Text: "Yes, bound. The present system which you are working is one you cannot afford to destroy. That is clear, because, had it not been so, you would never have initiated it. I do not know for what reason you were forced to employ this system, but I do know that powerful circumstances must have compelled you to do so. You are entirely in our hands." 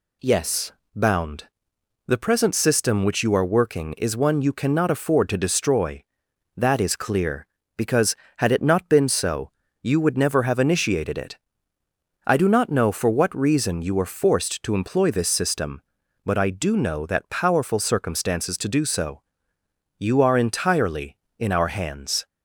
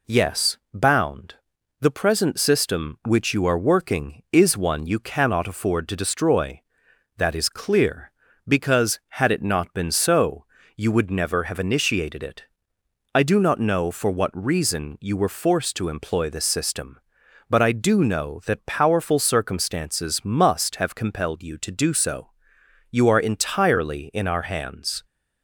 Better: second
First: skips "must have compelled you"; at 18.5 s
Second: none

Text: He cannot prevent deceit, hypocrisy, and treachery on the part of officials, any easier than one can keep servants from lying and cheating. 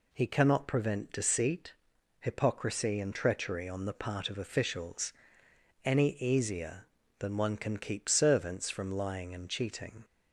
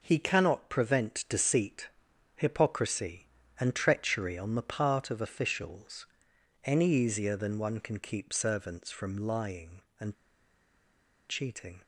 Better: first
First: none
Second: pauses between "and" and "cheating"; at 10.1 s; 1.1 s long

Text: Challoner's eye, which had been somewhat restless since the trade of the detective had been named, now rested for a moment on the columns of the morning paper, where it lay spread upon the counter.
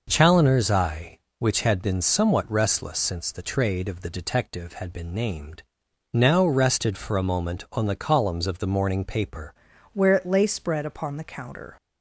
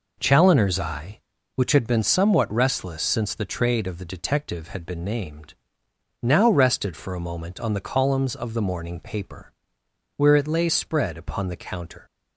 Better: second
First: changes voice at "where"; from 9.9 s on; 1.8 s long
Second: none

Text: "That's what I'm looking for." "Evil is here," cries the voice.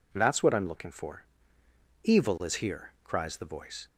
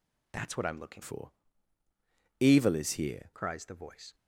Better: first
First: none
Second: changes voice from "for" to "here"; from 1.0 to 3.3 s; 2.3 s long

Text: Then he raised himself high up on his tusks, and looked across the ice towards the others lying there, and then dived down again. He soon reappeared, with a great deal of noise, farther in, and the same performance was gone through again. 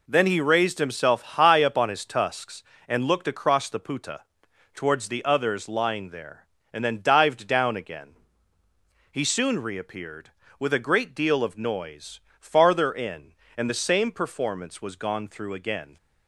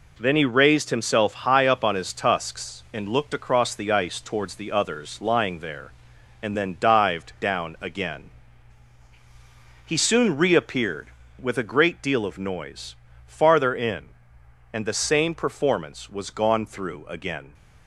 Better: second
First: says "puta" for "ice"; at 3.7 s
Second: none

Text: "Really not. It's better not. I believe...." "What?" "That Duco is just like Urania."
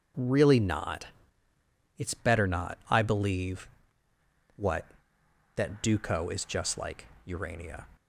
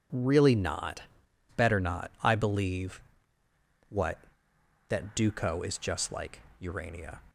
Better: first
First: pauses between "like" and "Urania"; slight; at 7.0 s; 0.18 s long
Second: skips "It's"; at 1.2 s // pauses between "like" and "Urania"; slight; at 6.4 s; 0.18 s long

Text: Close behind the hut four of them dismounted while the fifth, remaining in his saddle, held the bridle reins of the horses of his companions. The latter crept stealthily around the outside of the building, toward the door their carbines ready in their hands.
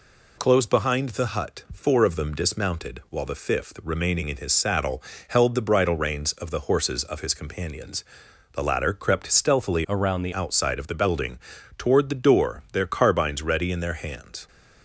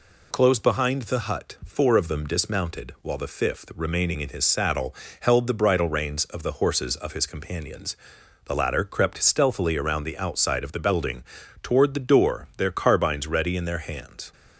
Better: second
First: changes voice from "around" to "the"; from 9.8 to 10.3 s; 0.5 s long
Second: none

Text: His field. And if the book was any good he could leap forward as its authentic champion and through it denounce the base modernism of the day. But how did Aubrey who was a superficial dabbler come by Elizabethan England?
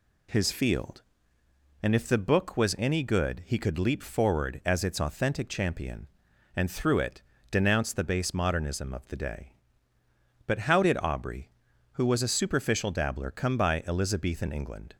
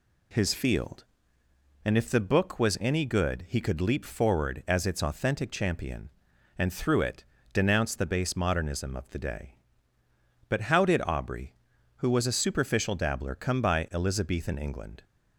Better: neither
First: pauses between "it" and "denounce"; slight; at 7.2 s; 0.26 s long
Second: pauses between "it" and "denounce"; slight; at 7.2 s; 0.26 s long

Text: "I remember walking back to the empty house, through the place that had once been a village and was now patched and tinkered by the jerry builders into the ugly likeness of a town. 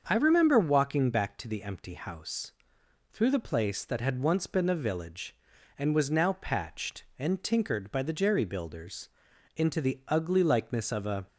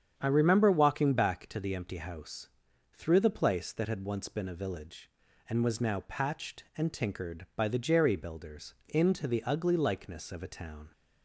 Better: second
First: starts louder than the rest; until 1.0 s; 6.5 dB // pauses between "builders" and "into"; noticeable; at 9.0 s; 0.46 s long // stops before "town"; at 11.2 s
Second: starts louder than the rest; strong; until 1.1 s; 8 dB

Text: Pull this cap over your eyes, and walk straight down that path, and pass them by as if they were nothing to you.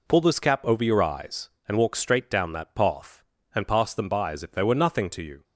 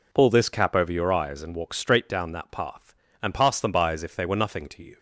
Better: neither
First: none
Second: none

